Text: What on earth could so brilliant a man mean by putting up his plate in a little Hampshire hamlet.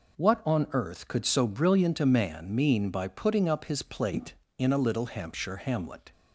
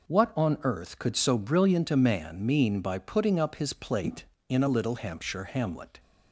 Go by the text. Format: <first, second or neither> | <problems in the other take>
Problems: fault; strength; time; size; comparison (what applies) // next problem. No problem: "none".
neither | none